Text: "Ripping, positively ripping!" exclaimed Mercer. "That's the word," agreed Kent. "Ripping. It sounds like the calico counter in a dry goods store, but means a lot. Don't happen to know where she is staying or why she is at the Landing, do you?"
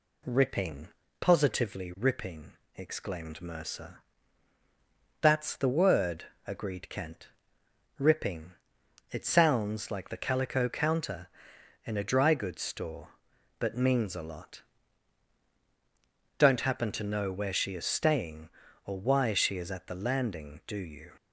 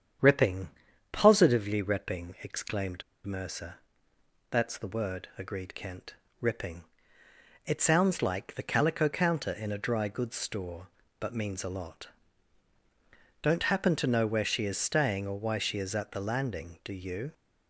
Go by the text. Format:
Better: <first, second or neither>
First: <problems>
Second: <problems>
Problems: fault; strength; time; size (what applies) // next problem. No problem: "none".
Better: first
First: none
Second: starts louder than the rest; strong; until 1.6 s; 8.5 dB // pauses between "exclaimed" and "Mercer"; slight; at 3.0 s; 0.24 s long